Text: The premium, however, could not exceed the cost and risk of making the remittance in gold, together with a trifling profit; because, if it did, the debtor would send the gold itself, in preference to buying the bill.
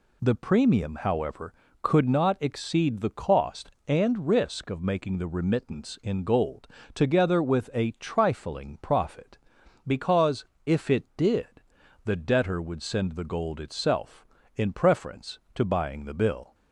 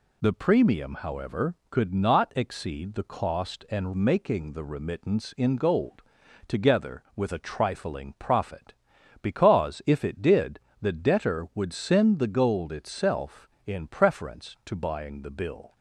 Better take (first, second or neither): first